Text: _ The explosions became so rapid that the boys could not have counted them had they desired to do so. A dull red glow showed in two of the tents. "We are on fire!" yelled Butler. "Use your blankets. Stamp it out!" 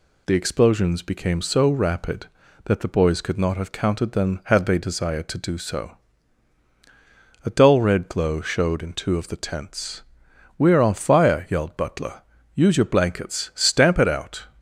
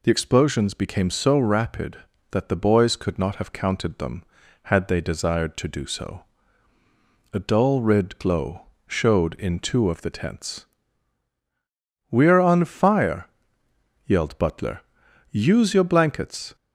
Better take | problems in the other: first | pauses between "glow" and "showed"; slight; at 8.6 s; 0.22 s long // stops before "Stamp it out"; at 16.5 s

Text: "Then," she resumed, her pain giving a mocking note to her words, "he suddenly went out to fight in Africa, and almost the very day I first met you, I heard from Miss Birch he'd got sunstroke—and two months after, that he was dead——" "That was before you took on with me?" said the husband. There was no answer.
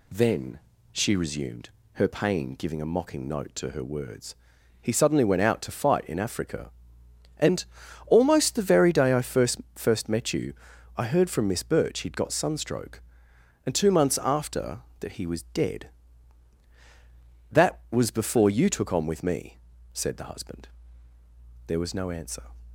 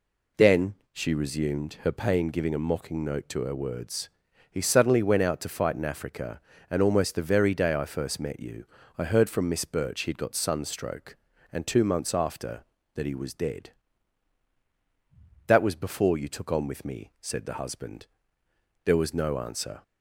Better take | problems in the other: second | pauses between "and" and "almost"; at 7.6 s; 0.40 s long // says "first" twice; at 9.7 s

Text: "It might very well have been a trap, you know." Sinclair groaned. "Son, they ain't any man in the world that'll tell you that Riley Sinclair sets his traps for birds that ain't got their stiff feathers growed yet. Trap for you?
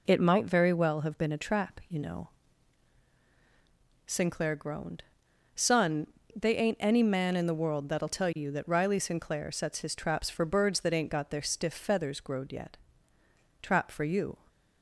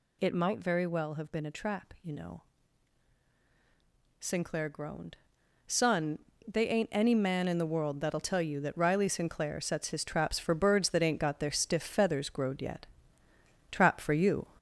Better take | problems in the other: first | gets louder; noticeable; throughout; 4.5 dB

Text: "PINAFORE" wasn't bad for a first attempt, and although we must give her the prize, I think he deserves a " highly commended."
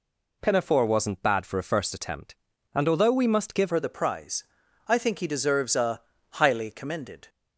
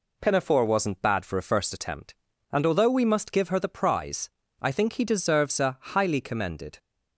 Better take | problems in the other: second | changes voice at "her"; from 3.6 s on; 3.6 s long

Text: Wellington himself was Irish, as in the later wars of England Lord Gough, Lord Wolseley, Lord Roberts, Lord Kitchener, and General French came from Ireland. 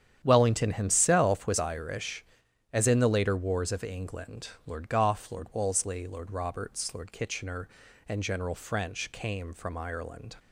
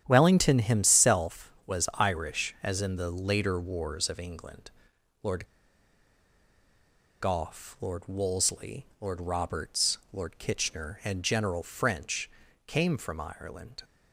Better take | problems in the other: first | starts louder than the rest; strong; until 1.0 s; 9.5 dB; strong in the first // pauses between "England" and "Lord"; noticeable; at 4.6 s; 0.54 s long; slight in the first // pauses between "Lord" and "Gough"; strong; at 5.4 s; 1.7 s long // pauses between "French" and "came"; slight; at 12.3 s; 0.34 s long

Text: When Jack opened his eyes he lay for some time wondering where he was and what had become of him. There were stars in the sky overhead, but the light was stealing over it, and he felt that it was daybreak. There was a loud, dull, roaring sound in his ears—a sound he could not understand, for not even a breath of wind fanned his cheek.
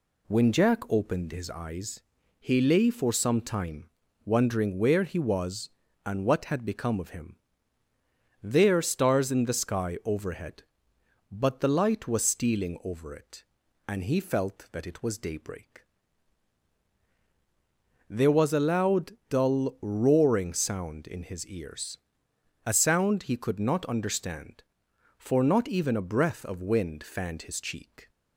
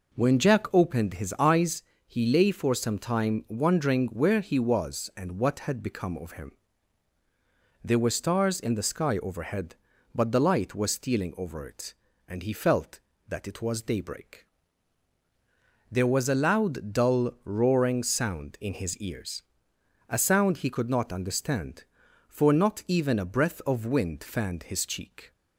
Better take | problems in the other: second | pauses between "eyes" and "he"; at 2.0 s; 0.38 s long; slight in the second // pauses between "time" and "wondering"; slight; at 3.8 s; 0.36 s long // skips "were"; at 8.8 s

